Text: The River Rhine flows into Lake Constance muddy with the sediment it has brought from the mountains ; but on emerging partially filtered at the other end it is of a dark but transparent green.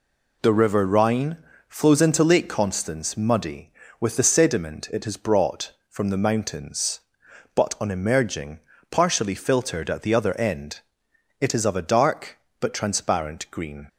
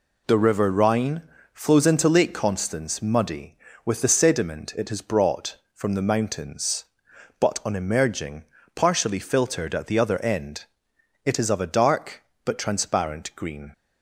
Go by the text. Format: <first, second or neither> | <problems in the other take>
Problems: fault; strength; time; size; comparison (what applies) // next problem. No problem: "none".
neither | pauses between "Rhine" and "flows"; slight; the same in both // pauses between "emerging" and "partially"; slight; the same in both // pauses between "end" and "it"; noticeable; the same in both